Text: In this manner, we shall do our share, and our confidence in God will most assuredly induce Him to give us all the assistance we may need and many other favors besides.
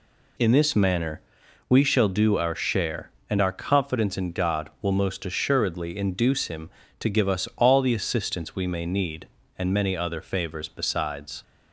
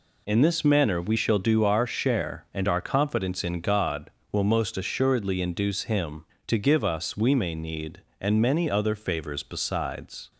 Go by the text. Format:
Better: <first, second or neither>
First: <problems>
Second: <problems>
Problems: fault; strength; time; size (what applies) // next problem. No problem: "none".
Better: first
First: none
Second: skips "all the assistance"; at 7.1 s